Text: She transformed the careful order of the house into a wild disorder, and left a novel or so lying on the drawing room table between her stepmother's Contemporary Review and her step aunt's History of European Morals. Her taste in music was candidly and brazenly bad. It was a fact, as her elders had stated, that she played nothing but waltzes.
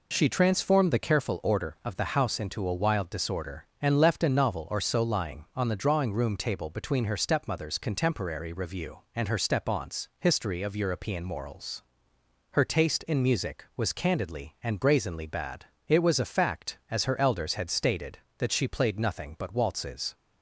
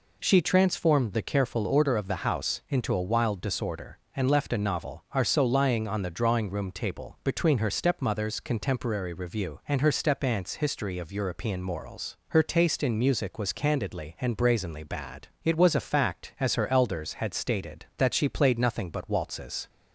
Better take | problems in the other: first | says "are" for "or"; at 5.1 s

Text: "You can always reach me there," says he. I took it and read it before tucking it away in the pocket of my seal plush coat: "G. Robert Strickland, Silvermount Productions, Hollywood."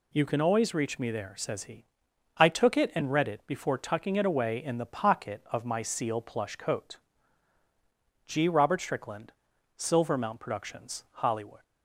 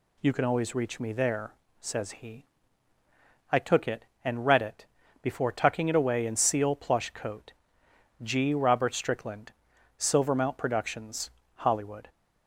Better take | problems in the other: first | pauses between "it" and "before"; slight; at 4.8 s; 0.36 s long // skips "the pocket of my"; at 6.3 s

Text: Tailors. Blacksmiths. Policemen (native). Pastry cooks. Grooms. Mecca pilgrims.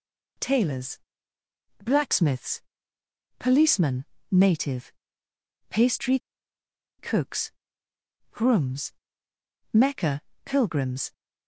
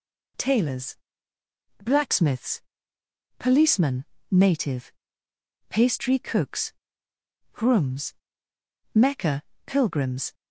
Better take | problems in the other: second | pauses between "Pastry" and "cooks"; noticeable; at 6.1 s; 0.80 s long // pauses between "Mecca" and "pilgrims"; slight; at 10.2 s; 0.24 s long; slight in the second

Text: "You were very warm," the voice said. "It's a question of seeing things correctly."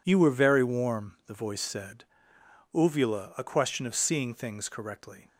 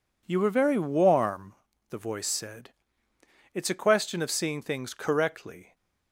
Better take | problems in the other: second | says "Uvula" for "It's"; at 2.7 s

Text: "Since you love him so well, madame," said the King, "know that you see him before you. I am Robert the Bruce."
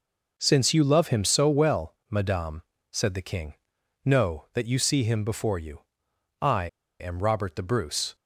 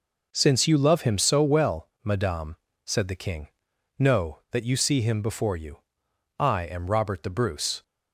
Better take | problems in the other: second | pauses between "I" and "am"; slight; at 6.6 s; 0.33 s long

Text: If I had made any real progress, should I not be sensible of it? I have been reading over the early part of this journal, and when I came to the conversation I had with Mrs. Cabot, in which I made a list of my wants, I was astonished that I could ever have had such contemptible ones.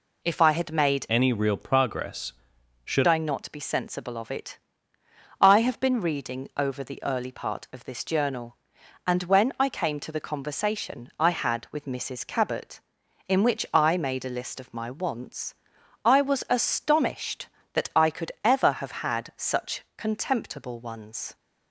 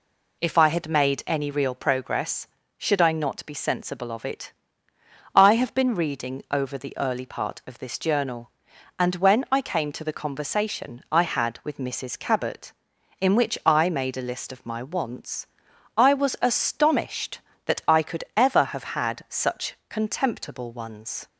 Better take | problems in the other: second | changes voice from "any" to "should"; from 1.0 to 3.0 s; 2.0 s long

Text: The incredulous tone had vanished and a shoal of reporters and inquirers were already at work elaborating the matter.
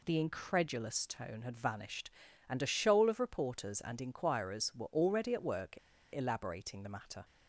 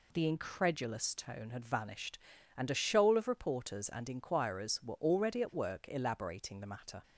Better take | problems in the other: second | pauses between "work" and "elaborating"; slight; at 5.7 s; 0.35 s long

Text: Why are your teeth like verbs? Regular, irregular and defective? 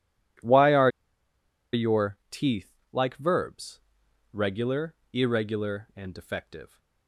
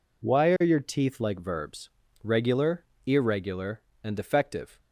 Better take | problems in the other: second | pauses between "are" and "your"; noticeable; at 0.8 s; 0.83 s long // pauses between "teeth" and "like"; slight; at 2.7 s; 0.20 s long

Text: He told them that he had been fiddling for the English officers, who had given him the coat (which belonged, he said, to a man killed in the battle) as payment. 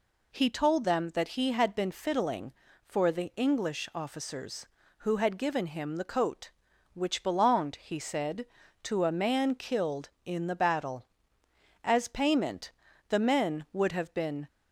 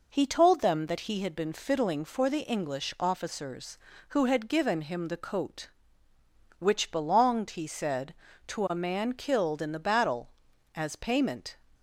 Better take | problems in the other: second | goes on to say "The men would have been"; from 13.0 s on; 1.3 s long

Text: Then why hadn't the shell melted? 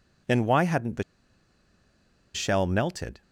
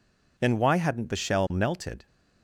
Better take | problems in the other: second | pauses between "the" and "shell"; strong; at 1.0 s; 1.3 s long

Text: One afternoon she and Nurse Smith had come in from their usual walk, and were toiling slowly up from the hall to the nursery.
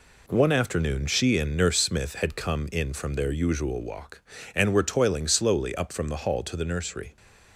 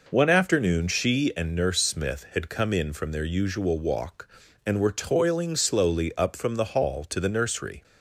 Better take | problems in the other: neither | none

